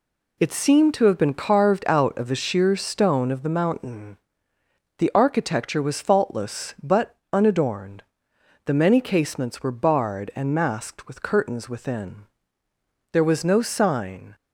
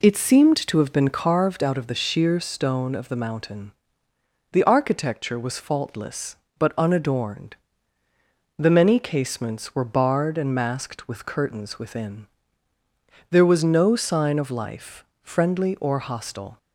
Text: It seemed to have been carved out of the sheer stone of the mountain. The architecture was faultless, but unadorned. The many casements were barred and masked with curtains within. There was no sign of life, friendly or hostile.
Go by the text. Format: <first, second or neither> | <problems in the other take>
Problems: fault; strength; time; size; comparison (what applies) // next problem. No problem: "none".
second | pauses between "but" and "unadorned"; slight; at 7.1 s; 0.18 s long // stops before "of life friendly or hostile"; at 14.3 s